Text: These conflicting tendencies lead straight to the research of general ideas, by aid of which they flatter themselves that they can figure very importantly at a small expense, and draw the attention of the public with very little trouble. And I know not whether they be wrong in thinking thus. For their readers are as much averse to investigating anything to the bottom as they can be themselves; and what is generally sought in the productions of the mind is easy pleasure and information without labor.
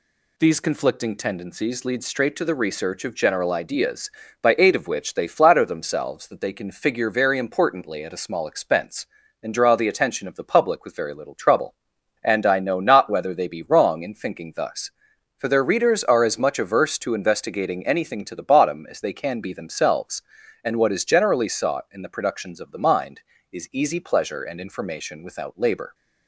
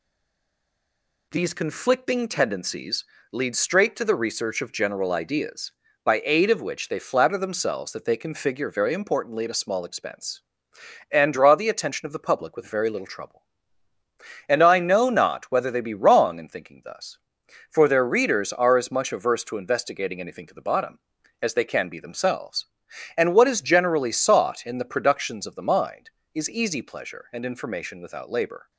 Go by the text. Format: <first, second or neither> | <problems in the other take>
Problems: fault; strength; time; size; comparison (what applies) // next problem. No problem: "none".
first | stays silent before the first word; noticeable; until 1.3 s; 1.3 s long // pauses between "tendencies" and "lead"; slight; at 3.0 s; 0.28 s long